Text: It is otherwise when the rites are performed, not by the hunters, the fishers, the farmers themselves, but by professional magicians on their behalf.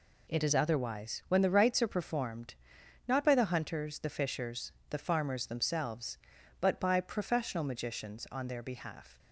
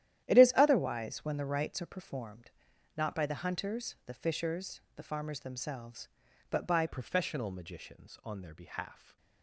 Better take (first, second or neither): first